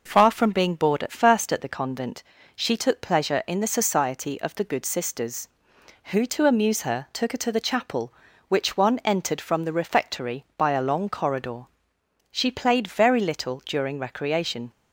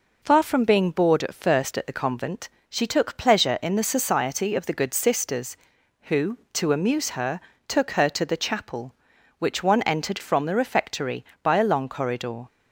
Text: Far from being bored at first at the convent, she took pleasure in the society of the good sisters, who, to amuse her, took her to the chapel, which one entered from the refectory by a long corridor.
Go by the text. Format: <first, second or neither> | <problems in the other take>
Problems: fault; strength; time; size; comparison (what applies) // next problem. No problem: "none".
second | goes on to say "She played very little during recreation"; strong; from 12.3 s on; 2.4 s long